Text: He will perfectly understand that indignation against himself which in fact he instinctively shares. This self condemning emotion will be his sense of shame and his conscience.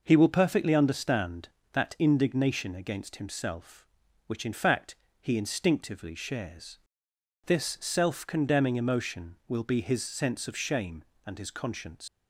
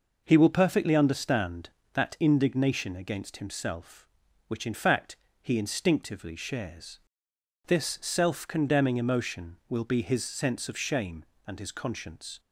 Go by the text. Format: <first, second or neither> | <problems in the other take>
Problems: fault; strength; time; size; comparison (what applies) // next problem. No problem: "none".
second | pauses between "fact" and "he"; slight; at 4.9 s; 0.26 s long; slight in the second // leaves "conscience" unfinished; at 12.0 s; 110 ms